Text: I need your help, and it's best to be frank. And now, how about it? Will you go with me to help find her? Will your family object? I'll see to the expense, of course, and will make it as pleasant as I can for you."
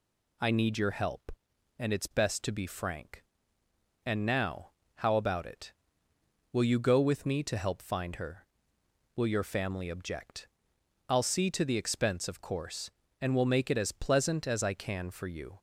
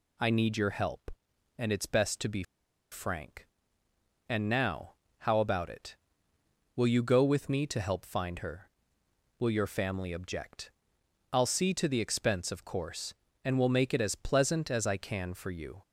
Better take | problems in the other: first | pauses between "be" and "frank"; noticeable; at 2.4 s; 0.48 s long

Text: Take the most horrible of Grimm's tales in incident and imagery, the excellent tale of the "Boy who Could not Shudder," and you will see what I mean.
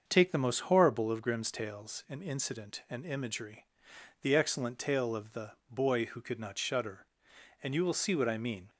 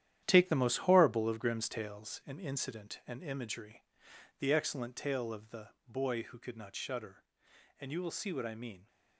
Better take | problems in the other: first | gets quieter; strong; throughout; 9 dB // starts louder than the rest; strong; until 1.2 s; 11 dB; also in the first // pauses between "the" and "Boy"; slight; at 5.6 s; 0.18 s long; slight in the first

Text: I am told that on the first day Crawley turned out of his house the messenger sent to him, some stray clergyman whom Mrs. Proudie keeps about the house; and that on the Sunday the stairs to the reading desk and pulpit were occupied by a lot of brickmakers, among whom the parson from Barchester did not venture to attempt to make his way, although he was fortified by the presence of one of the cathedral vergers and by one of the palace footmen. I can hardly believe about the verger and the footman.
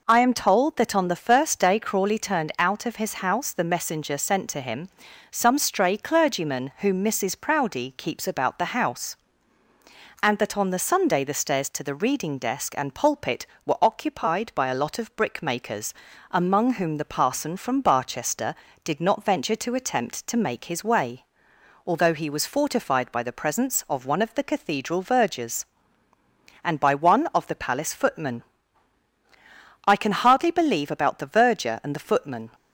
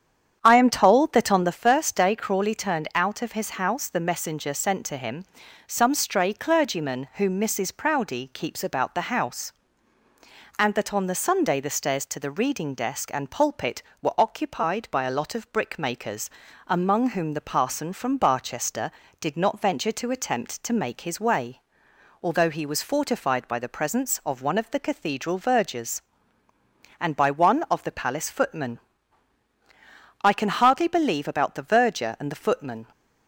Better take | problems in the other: first | starts louder than the rest; strong; until 1.6 s; 8.5 dB

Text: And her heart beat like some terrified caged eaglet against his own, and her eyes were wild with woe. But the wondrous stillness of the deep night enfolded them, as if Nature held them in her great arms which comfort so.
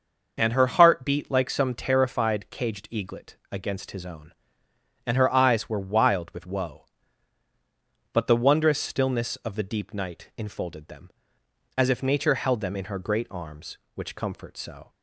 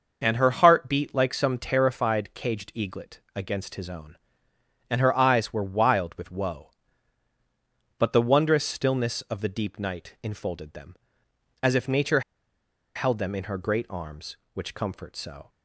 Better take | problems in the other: first | starts louder than the rest; noticeable; until 1.2 s; 6 dB; noticeable in the first // pauses between "eaglet" and "against"; slight; at 3.1 s; 0.16 s long; slight in the first // pauses between "Nature" and "held"; noticeable; at 12.2 s; 0.75 s long

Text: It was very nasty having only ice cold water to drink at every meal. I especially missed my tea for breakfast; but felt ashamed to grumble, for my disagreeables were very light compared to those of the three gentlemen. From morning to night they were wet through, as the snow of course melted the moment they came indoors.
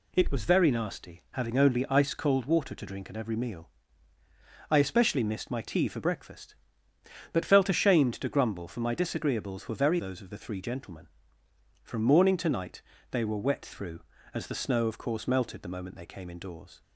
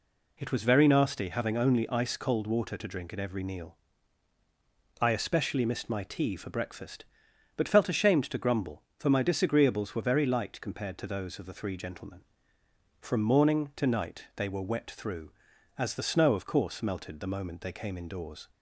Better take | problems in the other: second | skips "light compared to"; at 9.9 s // pauses between "night" and "they"; slight; at 12.8 s; 0.28 s long

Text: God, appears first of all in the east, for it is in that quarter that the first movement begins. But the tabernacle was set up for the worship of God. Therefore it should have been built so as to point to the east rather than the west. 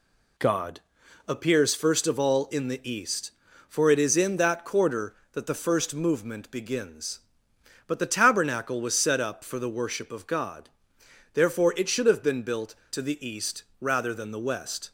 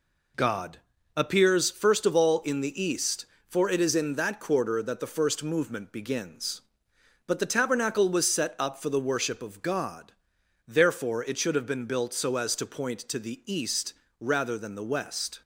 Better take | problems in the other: second | skips "so as to point"; at 12.8 s // pauses between "east" and "rather"; slight; at 13.6 s; 0.16 s long; slight in the second

